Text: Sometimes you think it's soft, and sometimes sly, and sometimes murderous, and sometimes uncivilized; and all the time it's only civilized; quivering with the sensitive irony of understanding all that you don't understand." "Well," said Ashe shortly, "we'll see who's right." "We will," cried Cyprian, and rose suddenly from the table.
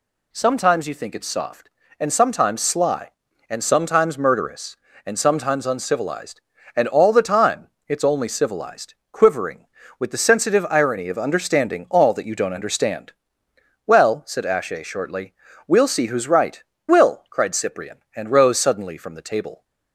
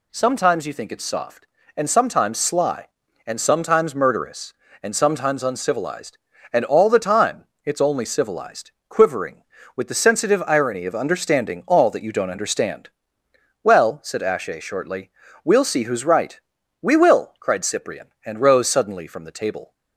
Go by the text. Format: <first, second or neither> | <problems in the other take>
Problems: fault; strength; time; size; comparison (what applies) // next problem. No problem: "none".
second | pauses between "time" and "it's"; slight; at 7.6 s; 0.22 s long; slight in the second // skips "We"; at 16.7 s